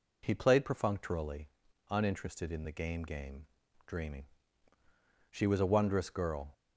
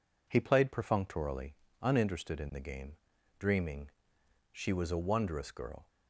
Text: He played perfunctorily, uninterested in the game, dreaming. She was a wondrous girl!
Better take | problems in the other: second | says "game" twice; at 3.0 s

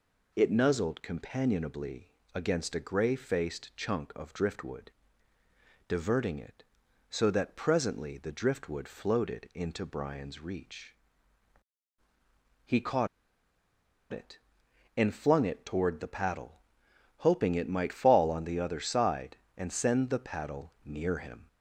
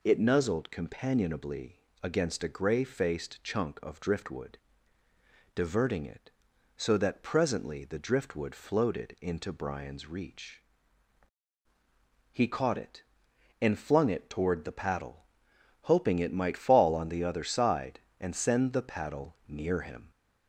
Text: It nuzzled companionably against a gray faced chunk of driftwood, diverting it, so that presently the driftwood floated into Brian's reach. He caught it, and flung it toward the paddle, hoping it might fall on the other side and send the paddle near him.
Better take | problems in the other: second | pauses between "companionably" and "against"; slight; at 2.1 s; 0.20 s long; slight in the second // pauses between "caught" and "it"; at 13.0 s; 1.0 s long

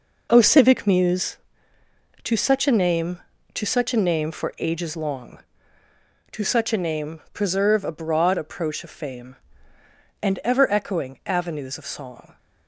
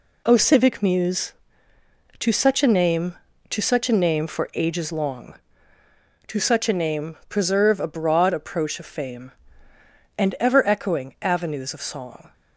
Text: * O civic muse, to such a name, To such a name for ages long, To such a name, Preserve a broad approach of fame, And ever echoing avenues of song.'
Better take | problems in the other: second | starts louder than the rest; noticeable; until 1.3 s; 5 dB

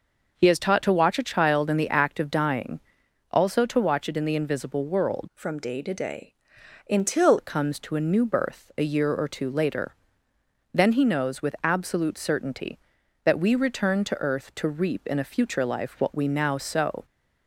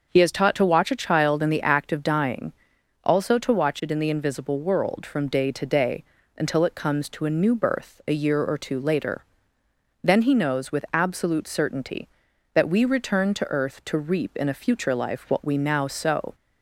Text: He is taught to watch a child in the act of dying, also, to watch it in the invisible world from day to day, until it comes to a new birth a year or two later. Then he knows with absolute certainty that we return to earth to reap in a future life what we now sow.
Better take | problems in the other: second | changes voice from "from" to "until"; from 5.3 to 7.3 s; 2.0 s long

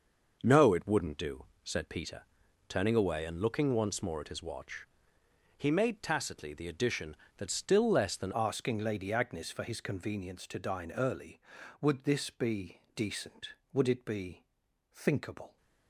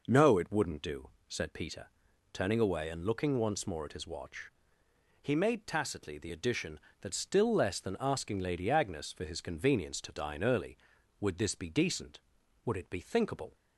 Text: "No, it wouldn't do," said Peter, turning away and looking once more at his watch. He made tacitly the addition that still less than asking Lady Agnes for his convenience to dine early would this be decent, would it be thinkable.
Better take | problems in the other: second | starts louder than the rest; noticeable; until 1.4 s; 6 dB // changes voice at "asking"; from 8.3 s on; 7.2 s long // pauses between "be" and "thinkable"; noticeable; at 14.4 s; 0.48 s long

